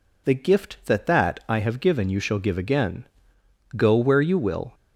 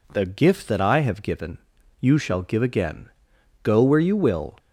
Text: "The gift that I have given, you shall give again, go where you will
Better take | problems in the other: second | says "that" twice; at 1.0 s

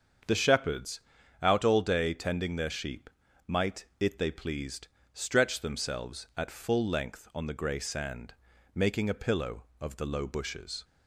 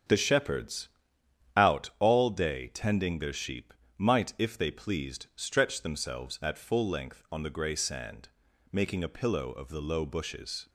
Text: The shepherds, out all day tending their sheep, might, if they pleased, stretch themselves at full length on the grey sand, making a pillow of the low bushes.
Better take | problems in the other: second | starts louder than the rest; until 1.6 s; 7 dB; strong in the second // says "it" for "if"; at 3.9 s

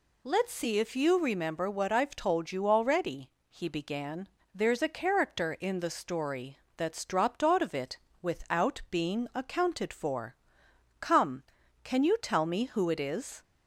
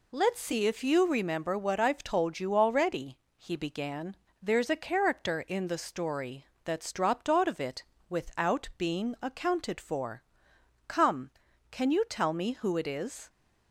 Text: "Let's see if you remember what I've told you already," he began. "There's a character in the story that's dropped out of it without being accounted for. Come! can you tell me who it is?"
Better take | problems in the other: first | gets quieter; noticeable; throughout; 4.5 dB // pauses between "story" and "that's"; slight; at 6.4 s; 0.18 s long; slight in the first // pauses between "it" and "without"; slight; at 7.8 s; 0.24 s long; slight in the first

